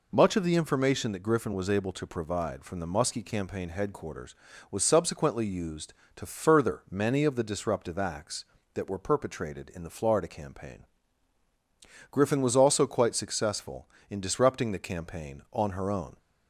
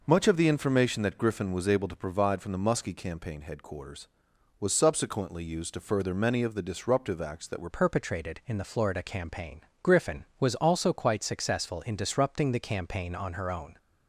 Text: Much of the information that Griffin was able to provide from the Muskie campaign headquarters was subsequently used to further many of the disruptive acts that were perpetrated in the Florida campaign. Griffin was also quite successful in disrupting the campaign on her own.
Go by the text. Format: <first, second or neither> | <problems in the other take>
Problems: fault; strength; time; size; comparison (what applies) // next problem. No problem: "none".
first | changes voice at "perpetrated"; from 7.7 s on; 6.0 s long